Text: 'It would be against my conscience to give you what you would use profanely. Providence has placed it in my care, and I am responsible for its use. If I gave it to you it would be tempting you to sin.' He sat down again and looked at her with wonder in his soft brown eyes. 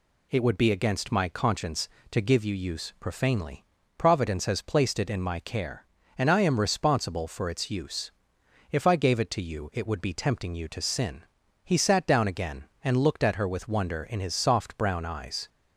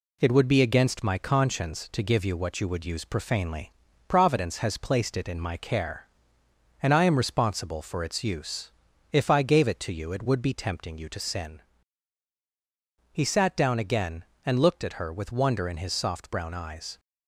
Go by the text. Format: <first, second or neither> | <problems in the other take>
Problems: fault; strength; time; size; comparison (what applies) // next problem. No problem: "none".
second | skips "what you would"; at 2.5 s